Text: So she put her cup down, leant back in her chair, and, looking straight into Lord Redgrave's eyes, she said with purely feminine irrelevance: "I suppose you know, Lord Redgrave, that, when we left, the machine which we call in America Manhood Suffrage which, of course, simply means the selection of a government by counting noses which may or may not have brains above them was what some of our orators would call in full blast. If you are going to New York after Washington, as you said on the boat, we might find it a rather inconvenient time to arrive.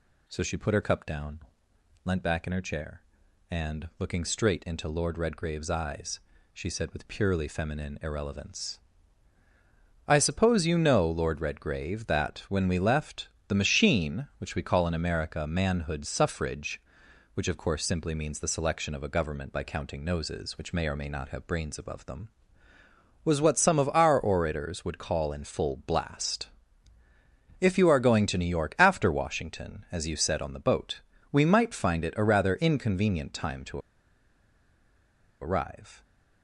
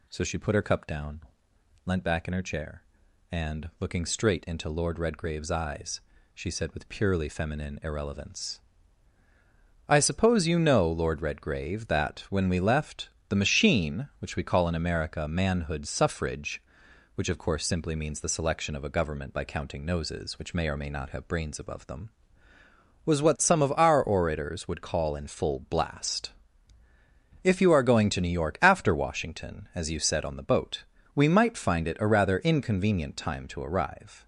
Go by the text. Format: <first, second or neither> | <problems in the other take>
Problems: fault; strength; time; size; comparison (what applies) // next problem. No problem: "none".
second | pauses between "to" and "arrive"; strong; at 33.7 s; 1.6 s long